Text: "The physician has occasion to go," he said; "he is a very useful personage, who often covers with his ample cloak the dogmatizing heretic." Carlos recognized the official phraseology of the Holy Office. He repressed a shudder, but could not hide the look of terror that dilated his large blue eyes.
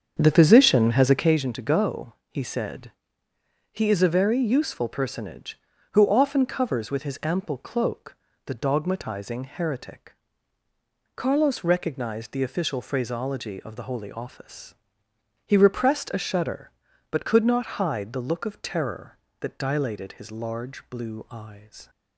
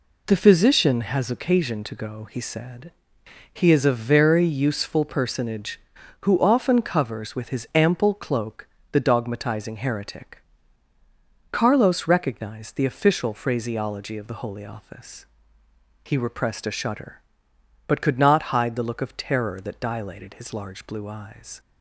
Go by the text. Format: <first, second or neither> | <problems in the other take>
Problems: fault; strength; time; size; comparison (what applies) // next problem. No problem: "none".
second | starts louder than the rest; strong; until 1.4 s; 7.5 dB // pauses between "cloak" and "the"; slight; at 8.1 s; 0.30 s long; slight in the second